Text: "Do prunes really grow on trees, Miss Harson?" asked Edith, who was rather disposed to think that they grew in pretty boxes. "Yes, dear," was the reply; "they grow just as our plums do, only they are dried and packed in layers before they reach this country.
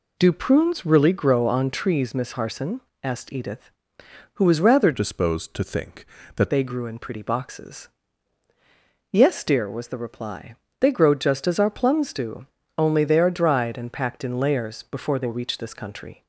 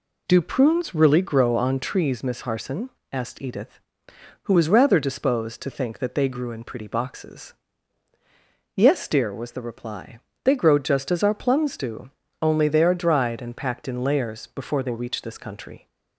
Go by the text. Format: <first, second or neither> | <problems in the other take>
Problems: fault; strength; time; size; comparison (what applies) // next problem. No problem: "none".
second | changes voice from "disposed" to "that"; from 4.9 to 6.5 s; 1.6 s long